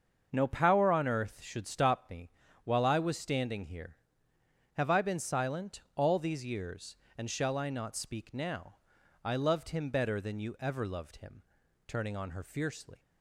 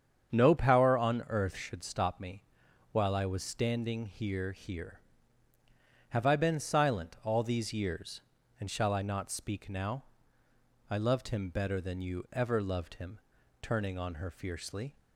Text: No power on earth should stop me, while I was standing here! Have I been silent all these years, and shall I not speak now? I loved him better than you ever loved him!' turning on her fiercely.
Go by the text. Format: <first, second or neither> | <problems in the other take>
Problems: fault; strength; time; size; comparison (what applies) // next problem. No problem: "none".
first | starts louder than the rest; strong; until 1.3 s; 7.5 dB; also in the first // says "here" twice; at 4.5 s